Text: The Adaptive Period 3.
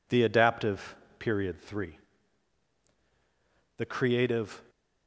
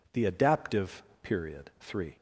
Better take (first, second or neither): second